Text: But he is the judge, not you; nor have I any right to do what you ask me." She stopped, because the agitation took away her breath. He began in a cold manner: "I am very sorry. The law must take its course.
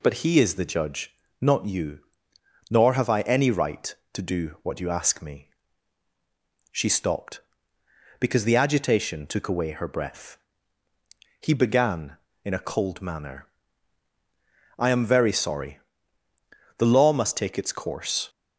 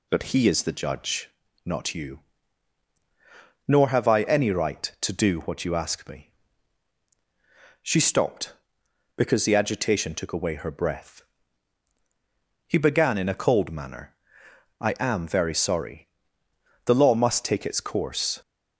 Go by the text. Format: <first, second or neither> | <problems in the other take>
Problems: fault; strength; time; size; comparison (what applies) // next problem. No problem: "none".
neither | none